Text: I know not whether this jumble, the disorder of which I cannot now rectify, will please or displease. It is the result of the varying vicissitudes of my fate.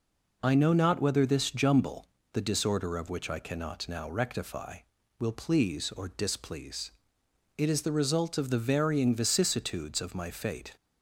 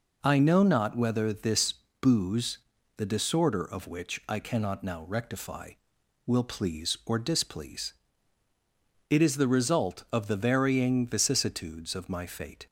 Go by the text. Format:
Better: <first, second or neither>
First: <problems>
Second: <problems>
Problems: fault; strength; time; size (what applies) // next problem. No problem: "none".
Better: first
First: none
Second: says "booze" for "jumble"; at 2.0 s